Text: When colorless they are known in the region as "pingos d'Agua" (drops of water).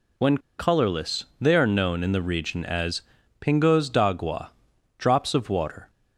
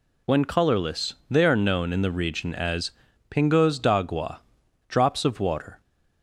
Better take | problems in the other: second | pauses between "When" and "colorless"; slight; at 0.3 s; 0.20 s long // pauses between "colorless" and "they"; slight; at 1.2 s; 0.16 s long; slight in the second // pauses between "as" and "pingos"; at 3.0 s; 0.40 s long; also in the second

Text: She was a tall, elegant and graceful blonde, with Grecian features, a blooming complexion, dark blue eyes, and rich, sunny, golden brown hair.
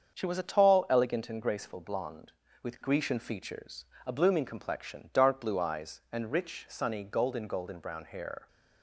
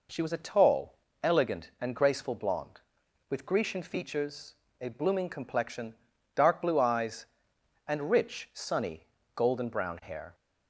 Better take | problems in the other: second | starts louder than the rest; until 1.2 s; 7 dB // says "golden" twice; at 7.4 s

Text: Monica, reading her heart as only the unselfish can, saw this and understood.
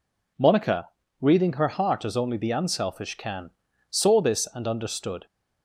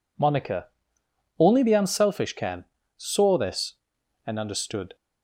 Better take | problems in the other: first | skips "reading her heart as"; at 1.0 s

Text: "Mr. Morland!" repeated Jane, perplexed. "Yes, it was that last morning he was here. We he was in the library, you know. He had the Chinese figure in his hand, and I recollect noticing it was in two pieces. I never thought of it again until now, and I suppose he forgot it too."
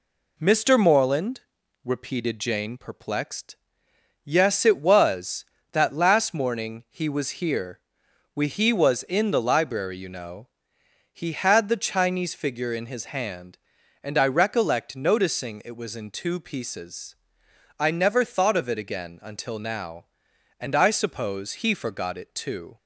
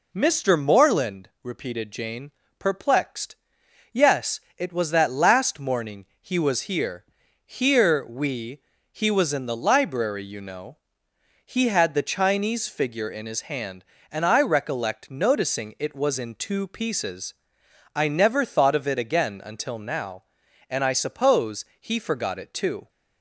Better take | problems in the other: first | pauses between "morning" and "he"; slight; at 6.0 s; 0.16 s long // says "here" twice; at 7.4 s // pauses between "We" and "he"; slight; at 8.6 s; 0.30 s long // pauses between "suppose" and "he"; slight; at 21.6 s; 0.16 s long

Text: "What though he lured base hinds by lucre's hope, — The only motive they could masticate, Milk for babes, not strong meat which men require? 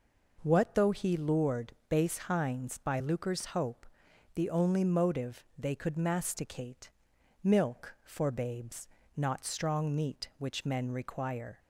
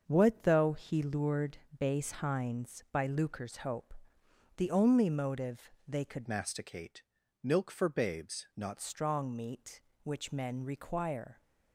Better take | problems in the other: first | starts louder than the rest; until 1.0 s; 6.5 dB // pauses between "lured" and "base"; slight; at 1.5 s; 0.22 s long // pauses between "motive" and "they"; slight; at 5.7 s; 0.16 s long // changes voice from "masticate" to "not"; from 6.2 to 8.7 s; 2.5 s long

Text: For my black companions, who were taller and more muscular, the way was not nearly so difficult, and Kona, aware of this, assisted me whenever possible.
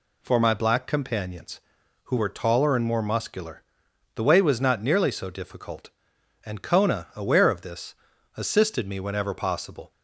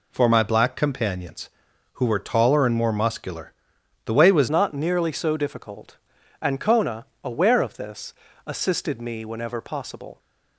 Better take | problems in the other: first | changes voice at "not"; from 4.5 s on; 5.6 s long

